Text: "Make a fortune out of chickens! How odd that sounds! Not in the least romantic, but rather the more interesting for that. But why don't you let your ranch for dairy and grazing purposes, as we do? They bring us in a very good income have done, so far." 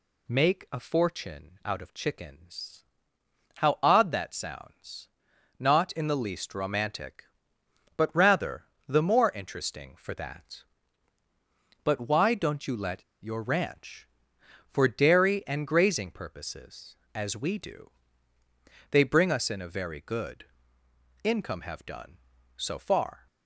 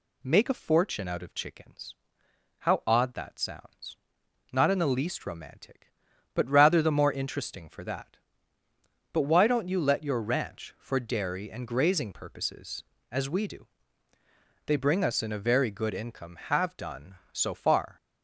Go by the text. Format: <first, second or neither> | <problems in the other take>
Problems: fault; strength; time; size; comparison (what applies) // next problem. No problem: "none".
second | pauses between "rather" and "the"; slight; at 8.6 s; 0.24 s long // pauses between "let" and "your"; slight; at 13.0 s; 0.18 s long // pauses between "good" and "income"; noticeable; at 20.4 s; 0.76 s long